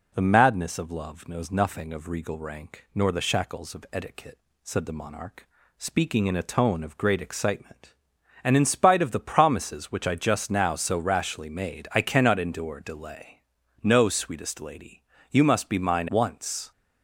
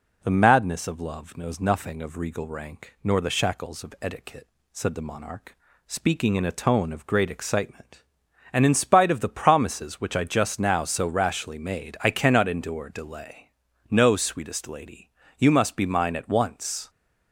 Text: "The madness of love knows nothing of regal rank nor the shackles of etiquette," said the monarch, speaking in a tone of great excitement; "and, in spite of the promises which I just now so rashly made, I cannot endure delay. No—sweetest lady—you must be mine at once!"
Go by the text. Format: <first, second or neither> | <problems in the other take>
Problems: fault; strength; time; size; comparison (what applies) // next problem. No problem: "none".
second | skips "at"; at 16.0 s